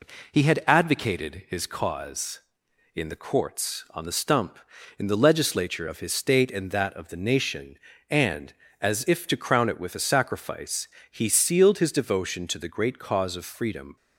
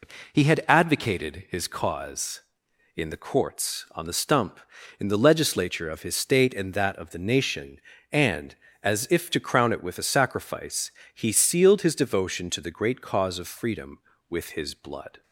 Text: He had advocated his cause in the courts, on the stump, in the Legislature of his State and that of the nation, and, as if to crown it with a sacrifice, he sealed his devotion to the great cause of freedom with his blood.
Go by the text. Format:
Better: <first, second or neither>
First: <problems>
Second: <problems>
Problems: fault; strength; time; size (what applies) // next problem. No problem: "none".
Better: second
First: stops before "with his blood"; at 13.9 s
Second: none